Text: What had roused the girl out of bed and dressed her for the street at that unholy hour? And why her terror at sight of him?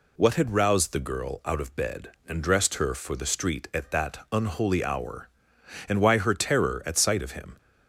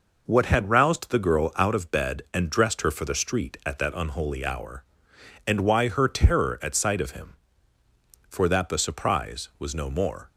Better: first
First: none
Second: goes on to say "For that the surprise was no more"; strong; from 8.2 s on; 2.0 s long

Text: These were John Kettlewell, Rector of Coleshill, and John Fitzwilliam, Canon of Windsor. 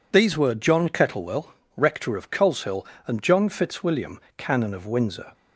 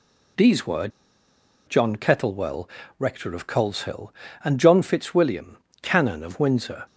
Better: first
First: none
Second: pauses between "were" and "John"; noticeable; at 0.8 s; 0.80 s long

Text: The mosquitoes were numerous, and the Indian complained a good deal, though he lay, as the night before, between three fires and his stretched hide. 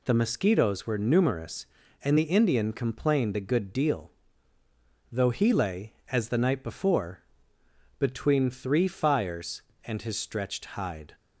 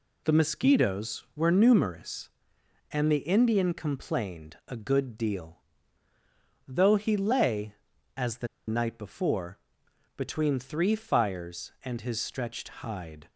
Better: first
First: none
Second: pauses between "the" and "night"; slight; at 8.4 s; 0.20 s long // pauses between "stretched" and "hide"; slight; at 12.6 s; 0.16 s long

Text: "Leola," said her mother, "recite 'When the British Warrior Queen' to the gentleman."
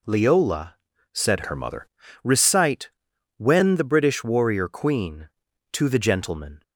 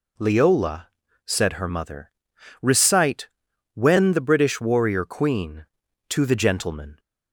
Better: second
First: changes voice from "her" to "mother"; from 1.4 to 1.8 s; 0.4 s long // pauses between "recite" and "When"; noticeable; at 2.8 s; 0.48 s long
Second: pauses between "recite" and "When"; noticeable; at 3.2 s; 0.46 s long

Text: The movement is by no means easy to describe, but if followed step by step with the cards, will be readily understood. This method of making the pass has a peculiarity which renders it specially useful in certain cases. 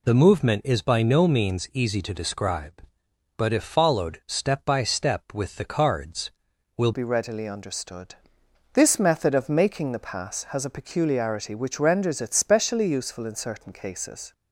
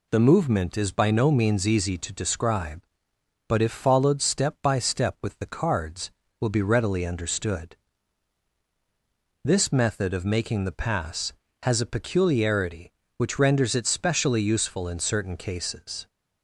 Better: second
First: changes voice at "be"; from 6.9 s on; 7.4 s long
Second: none

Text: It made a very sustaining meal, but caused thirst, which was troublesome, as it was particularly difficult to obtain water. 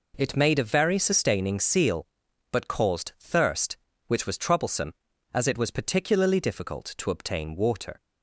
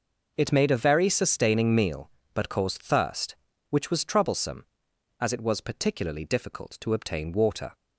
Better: second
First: says "seal" for "meal"; at 1.5 s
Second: none

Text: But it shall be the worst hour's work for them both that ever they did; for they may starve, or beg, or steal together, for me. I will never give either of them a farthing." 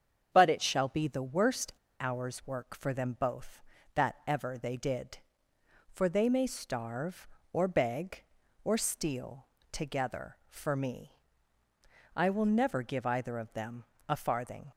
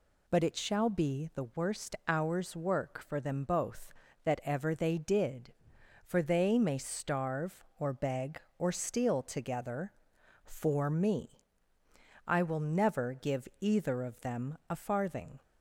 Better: second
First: starts louder than the rest; strong; until 1.3 s; 7.5 dB // pauses between "worst" and "hour's"; slight; at 1.7 s; 0.27 s long // pauses between "steal" and "together"; slight; at 9.4 s; 0.26 s long // pauses between "them" and "a"; slight; at 13.8 s; 0.24 s long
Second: none

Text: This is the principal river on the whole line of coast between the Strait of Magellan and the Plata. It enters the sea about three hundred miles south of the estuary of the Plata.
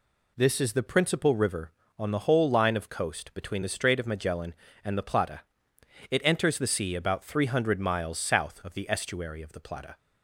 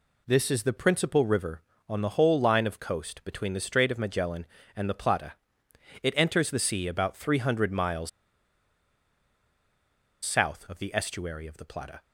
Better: first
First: none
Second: pauses between "miles" and "south"; strong; at 8.0 s; 2.1 s long

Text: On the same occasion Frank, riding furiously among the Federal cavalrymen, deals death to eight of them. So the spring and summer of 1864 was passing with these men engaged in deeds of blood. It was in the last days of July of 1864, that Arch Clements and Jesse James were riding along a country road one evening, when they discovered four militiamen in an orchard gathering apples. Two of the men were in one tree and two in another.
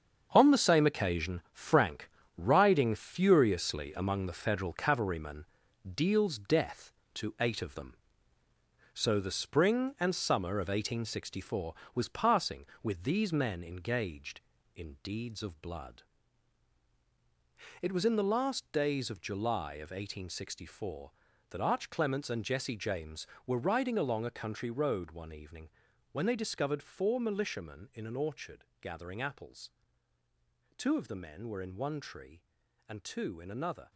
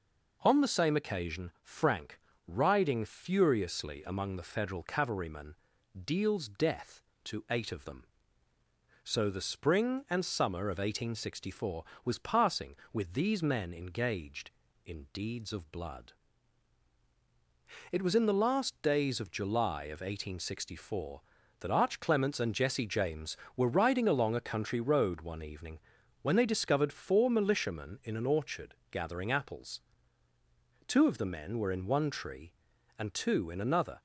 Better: second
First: gets quieter; strong; throughout; 9.5 dB // pauses between "orchard" and "gathering"; slight; at 28.6 s; 0.16 s long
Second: pauses between "orchard" and "gathering"; slight; at 28.7 s; 0.16 s long

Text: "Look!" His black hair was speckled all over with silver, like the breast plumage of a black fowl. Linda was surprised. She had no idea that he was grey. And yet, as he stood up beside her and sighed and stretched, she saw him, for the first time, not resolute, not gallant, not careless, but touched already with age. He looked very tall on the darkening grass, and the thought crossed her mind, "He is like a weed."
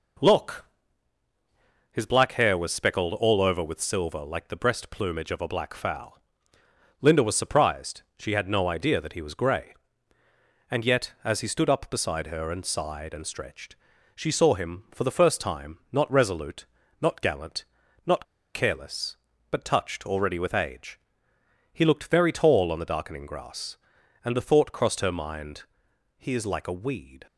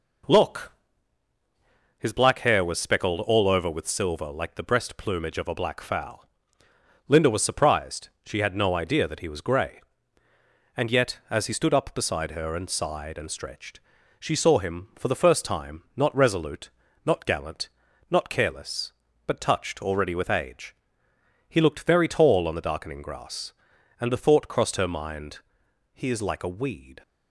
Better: second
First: pauses between "not" and "careless"; slight; at 18.2 s; 0.28 s long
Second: none

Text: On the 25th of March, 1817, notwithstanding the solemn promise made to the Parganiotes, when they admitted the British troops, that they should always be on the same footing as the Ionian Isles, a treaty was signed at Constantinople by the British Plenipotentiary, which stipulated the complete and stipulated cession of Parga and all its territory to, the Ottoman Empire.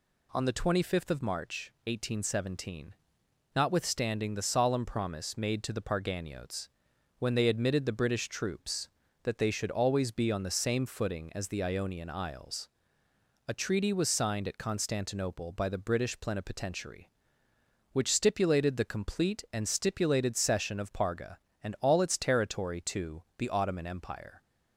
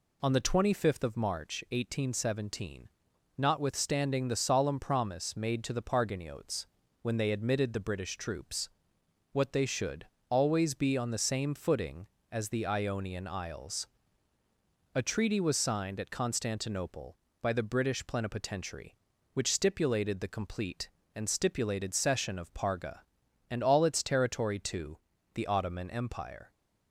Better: first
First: none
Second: says "what" for "that"; at 9.3 s // pauses between "should" and "always"; slight; at 10.0 s; 0.24 s long

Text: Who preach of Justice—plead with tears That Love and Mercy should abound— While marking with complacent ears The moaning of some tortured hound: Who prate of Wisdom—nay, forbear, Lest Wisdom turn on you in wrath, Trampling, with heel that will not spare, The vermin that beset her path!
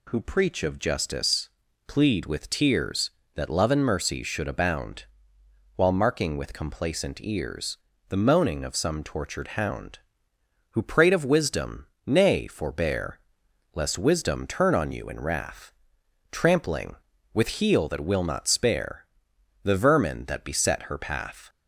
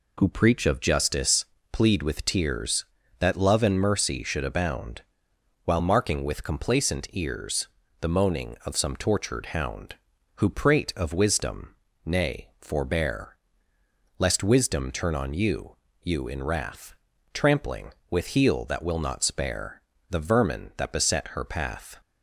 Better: first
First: pauses between "ears" and "The"; slight; at 7.7 s; 0.30 s long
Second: pauses between "ears" and "The"; slight; at 7.6 s; 0.32 s long // says "you" twice; at 16.0 s

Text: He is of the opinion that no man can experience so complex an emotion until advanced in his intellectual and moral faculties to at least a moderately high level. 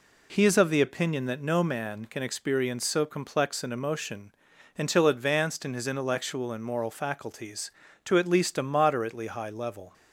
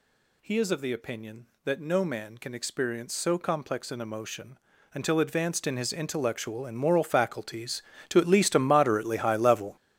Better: first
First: pauses between "emotion" and "until"; noticeable; at 4.3 s; 0.46 s long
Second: gets louder; strong; throughout; 12.5 dB // pauses between "emotion" and "until"; slight; at 4.5 s; 0.36 s long

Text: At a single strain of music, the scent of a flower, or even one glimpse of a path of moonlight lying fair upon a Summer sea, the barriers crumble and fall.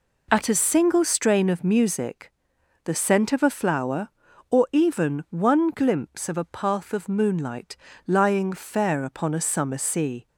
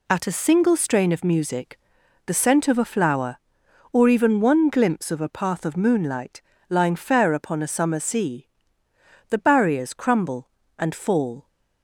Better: second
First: pauses between "moonlight" and "lying"; slight; at 7.7 s; 0.30 s long // stops before "the barriers crumble and fall"; at 10.2 s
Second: pauses between "moonlight" and "lying"; slight; at 6.4 s; 0.28 s long

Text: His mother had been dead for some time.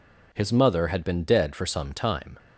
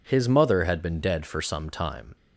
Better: neither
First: none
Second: none

